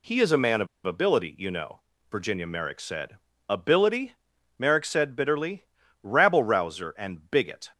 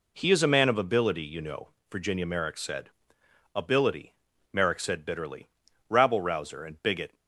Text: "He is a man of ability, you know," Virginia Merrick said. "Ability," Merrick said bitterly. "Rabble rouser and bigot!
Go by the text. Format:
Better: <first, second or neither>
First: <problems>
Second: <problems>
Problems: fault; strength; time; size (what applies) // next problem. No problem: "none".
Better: second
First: pauses between "of" and "ability"; slight; at 0.6 s; 0.18 s long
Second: none